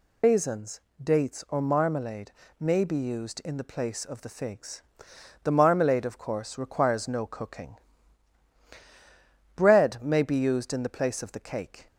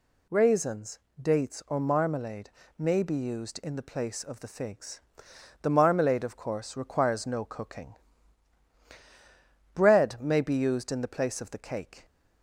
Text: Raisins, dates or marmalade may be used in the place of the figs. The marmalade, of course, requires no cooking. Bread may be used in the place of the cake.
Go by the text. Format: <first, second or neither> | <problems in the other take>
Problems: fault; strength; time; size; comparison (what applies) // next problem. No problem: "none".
second | loses the start of "Raisins"; at 0.2 s; 120 ms // pauses between "marmalade" and "may"; slight; at 2.3 s; 0.28 s long; slight in the second